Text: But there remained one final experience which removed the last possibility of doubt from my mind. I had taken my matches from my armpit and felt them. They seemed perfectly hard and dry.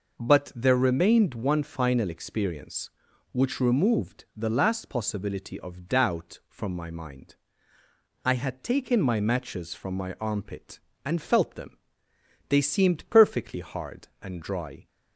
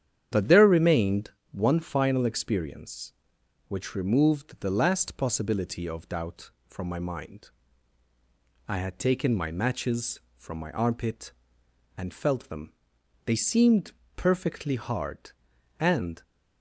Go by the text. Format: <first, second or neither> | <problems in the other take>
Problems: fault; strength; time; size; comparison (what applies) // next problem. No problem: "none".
first | starts louder than the rest; strong; until 1.5 s; 9.5 dB // pauses between "remained" and "one"; slight; at 1.2 s; 0.22 s long // pauses between "seemed" and "perfectly"; slight; at 13.9 s; 0.24 s long // stops before "dry"; at 16.2 s